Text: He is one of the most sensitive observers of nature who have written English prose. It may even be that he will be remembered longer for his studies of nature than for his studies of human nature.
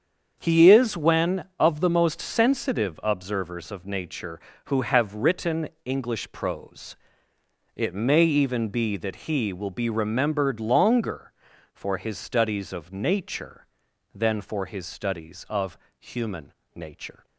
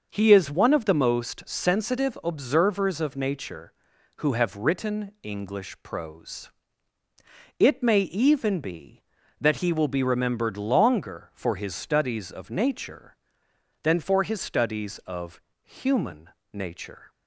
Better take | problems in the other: second | starts louder than the rest; strong; until 1.4 s; 7.5 dB; noticeable in the second // says "when" for "one"; at 0.9 s // pauses between "written" and "English"; slight; at 5.6 s; 0.16 s long // pauses between "of" and "human"; slight; at 15.7 s; 0.22 s long; slight in the second // pauses between "human" and "nature"; slight; at 16.5 s; 0.22 s long; slight in the second

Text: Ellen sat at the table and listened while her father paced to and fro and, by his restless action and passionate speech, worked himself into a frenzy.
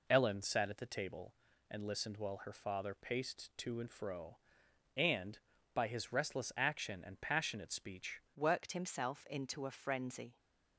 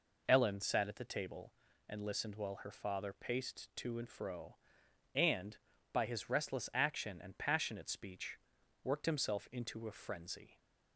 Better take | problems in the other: second | changes voice at "worked"; from 8.3 s on; 2.0 s long

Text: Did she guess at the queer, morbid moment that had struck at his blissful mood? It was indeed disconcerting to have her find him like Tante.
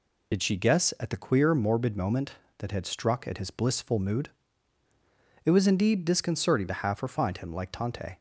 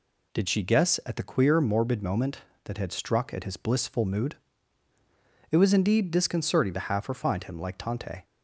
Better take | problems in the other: second | loses the start of "Did"; at 0.3 s; 60 ms

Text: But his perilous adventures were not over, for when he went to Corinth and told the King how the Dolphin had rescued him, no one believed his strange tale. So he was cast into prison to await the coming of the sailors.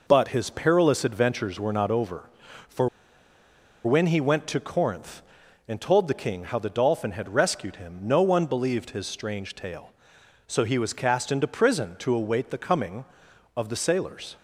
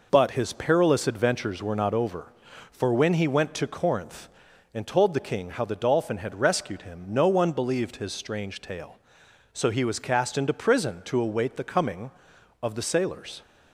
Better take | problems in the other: second | pauses between "for" and "when"; noticeable; at 2.8 s; 0.96 s long

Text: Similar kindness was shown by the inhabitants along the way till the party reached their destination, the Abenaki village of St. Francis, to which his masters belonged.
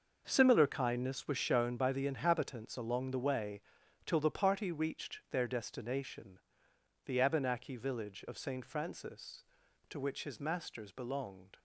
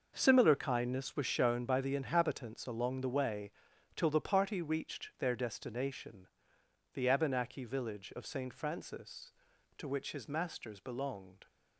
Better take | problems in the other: neither | pauses between "way" and "till"; noticeable; the same in both

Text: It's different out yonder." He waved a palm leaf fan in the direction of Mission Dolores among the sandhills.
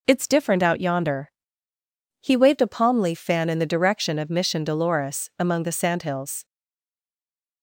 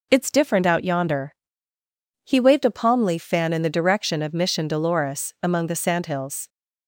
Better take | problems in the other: second | stays silent after the last word; noticeable; from 6.4 s on; 1.2 s long

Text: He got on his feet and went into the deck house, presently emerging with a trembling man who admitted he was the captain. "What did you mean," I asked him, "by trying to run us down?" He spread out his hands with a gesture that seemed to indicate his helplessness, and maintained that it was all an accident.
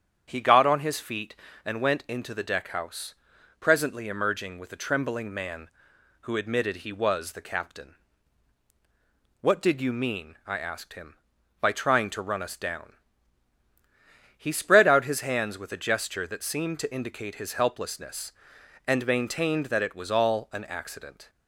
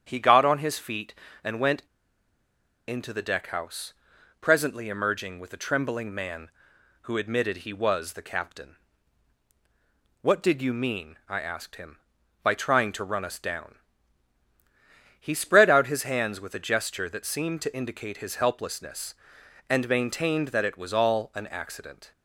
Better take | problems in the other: first | starts louder than the rest; strong; until 1.0 s; 8 dB; strong in the first // pauses between "went" and "into"; at 1.8 s; 1.0 s long

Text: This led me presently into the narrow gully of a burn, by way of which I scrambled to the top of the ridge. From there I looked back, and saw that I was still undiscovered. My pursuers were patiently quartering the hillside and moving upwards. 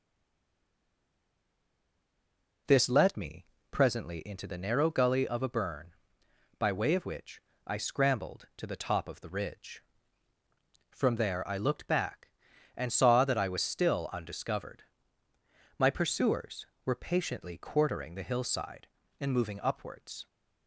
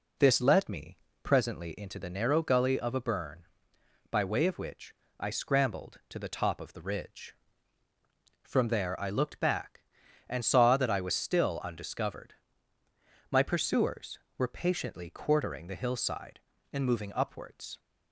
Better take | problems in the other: second | stays silent before the first word; strong; until 2.6 s; 2.6 s long // pauses between "me" and "presently"; slight; at 3.4 s; 0.24 s long; slight in the second // pauses between "which" and "I"; slight; at 7.4 s; 0.26 s long; slight in the second

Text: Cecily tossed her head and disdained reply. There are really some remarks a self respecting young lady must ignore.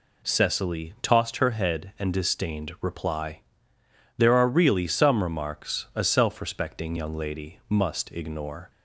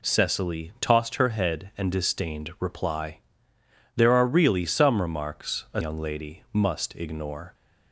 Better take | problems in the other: first | skips "self respecting"; at 5.8 s

